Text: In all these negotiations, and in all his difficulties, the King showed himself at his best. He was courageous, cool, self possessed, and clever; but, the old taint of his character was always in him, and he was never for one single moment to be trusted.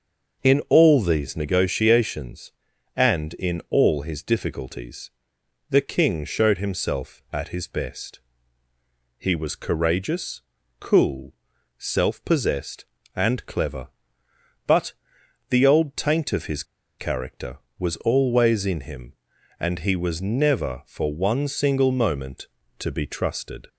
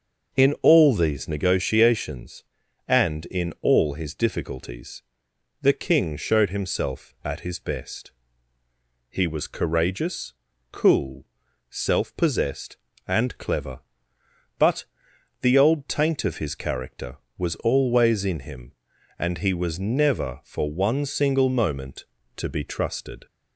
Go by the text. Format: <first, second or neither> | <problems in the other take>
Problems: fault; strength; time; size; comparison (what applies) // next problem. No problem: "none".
second | starts louder than the rest; noticeable; until 1.5 s; 6 dB; noticeable in the second // pauses between "his" and "character"; slight; at 16.6 s; 0.35 s long